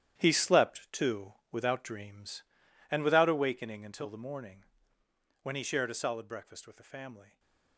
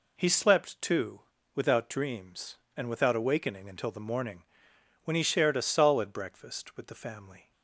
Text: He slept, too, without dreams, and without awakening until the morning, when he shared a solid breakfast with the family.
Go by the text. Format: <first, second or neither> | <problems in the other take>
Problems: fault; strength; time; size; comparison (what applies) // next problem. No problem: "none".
second | gets quieter; strong; throughout; 12.5 dB // stays silent after the last word; slight; from 7.2 s on; 0.5 s long